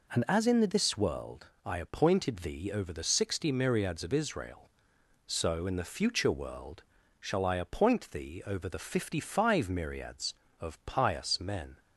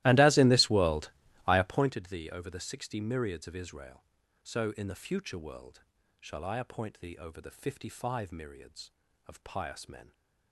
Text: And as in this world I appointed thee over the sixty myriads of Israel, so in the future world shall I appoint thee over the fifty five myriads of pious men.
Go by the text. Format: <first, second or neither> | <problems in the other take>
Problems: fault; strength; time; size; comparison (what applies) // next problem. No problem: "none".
first | starts louder than the rest; strong; until 1.9 s; 16.5 dB // pauses between "world" and "I"; slight; at 1.1 s; 0.36 s long; slight in the first // pauses between "world" and "shall"; at 5.8 s; 0.40 s long; also in the first